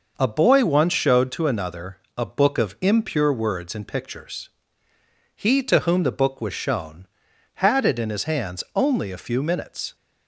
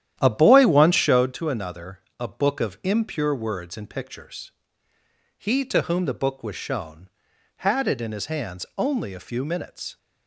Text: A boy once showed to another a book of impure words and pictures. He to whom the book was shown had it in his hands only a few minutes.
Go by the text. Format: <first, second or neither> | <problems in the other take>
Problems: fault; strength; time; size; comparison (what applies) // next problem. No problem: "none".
first | starts louder than the rest; strong; until 1.3 s; 11 dB // pauses between "another" and "a"; slight; at 1.9 s; 0.20 s long; slight in the first